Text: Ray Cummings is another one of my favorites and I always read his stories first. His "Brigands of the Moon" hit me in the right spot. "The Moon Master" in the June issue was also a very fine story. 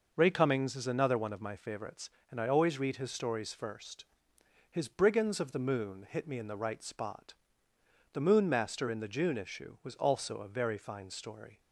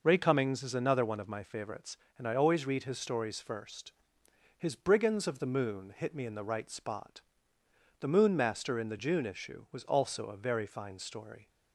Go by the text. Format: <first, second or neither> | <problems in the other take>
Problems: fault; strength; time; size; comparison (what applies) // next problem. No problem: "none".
neither | none